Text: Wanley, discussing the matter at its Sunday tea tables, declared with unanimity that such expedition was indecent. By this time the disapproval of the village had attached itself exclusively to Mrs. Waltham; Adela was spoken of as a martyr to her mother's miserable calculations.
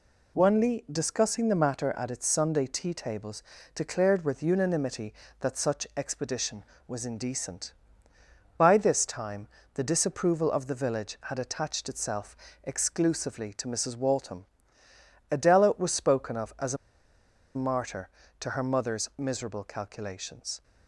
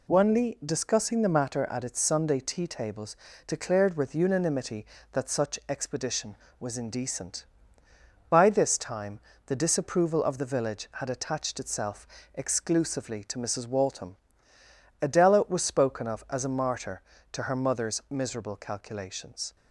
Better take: second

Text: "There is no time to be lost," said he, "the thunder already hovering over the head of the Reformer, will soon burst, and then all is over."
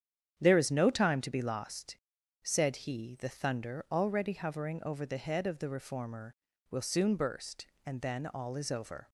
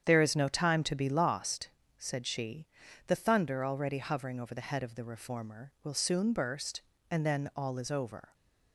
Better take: first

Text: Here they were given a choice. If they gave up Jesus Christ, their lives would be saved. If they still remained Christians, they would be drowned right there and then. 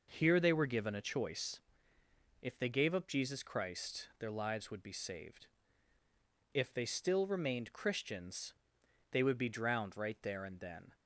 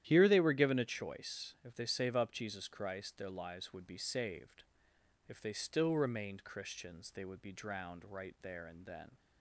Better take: first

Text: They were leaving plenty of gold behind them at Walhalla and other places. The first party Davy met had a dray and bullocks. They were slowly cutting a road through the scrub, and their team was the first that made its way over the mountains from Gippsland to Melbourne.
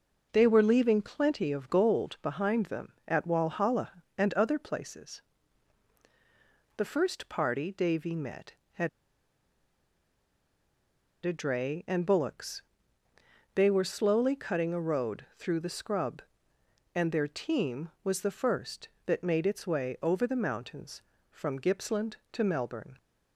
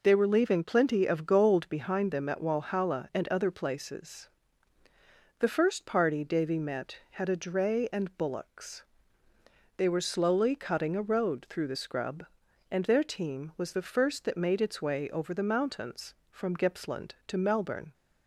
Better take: second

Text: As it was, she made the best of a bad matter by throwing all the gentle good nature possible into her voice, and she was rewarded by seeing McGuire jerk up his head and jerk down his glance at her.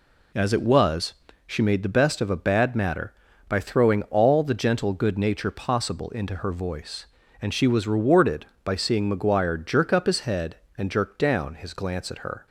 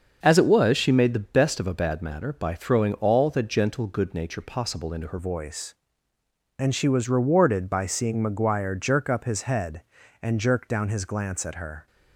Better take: first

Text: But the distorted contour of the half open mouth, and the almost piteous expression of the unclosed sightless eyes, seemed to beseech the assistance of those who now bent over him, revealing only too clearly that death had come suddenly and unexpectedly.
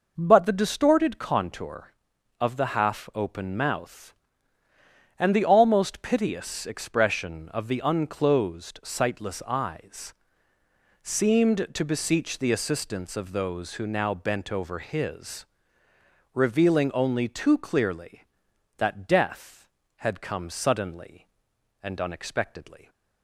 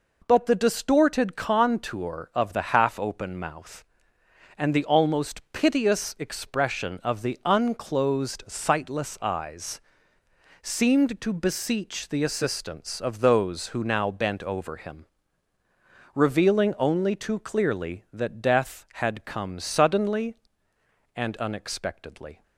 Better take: second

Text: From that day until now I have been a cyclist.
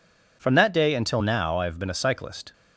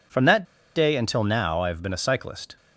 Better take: first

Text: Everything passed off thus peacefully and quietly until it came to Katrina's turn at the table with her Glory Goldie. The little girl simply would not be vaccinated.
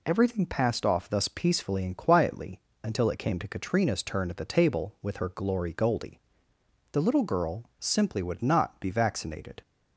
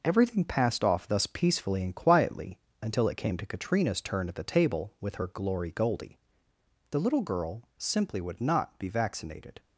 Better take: first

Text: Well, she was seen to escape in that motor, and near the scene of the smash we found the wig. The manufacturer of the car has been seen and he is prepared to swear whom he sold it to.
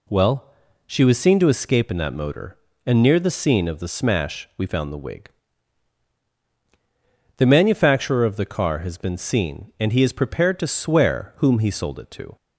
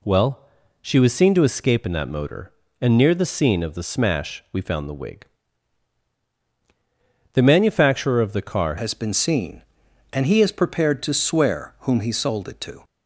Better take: first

